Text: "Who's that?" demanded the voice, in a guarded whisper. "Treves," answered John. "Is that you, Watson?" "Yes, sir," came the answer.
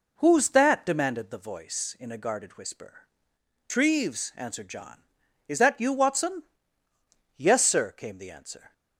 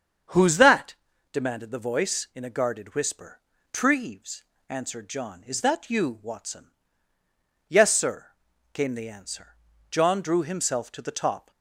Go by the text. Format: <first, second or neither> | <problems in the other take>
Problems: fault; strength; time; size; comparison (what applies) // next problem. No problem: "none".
first | starts louder than the rest; strong; until 1.7 s; 7.5 dB // goes on to say "John drew himself to the top"; from 9.9 s on; 1.6 s long